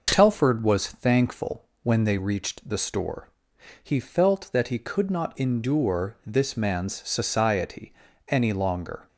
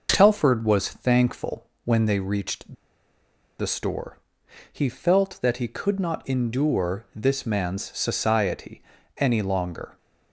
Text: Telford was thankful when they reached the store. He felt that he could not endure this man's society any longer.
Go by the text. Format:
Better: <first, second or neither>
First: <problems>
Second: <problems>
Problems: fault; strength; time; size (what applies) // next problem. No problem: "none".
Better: first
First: pauses between "thankful" and "when"; slight; at 1.6 s; 0.16 s long // pauses between "society" and "any"; slight; at 7.9 s; 0.36 s long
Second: pauses between "thankful" and "when"; slight; at 1.6 s; 0.16 s long // pauses between "reached" and "the"; noticeable; at 2.7 s; 0.85 s long // pauses between "society" and "any"; slight; at 8.8 s; 0.36 s long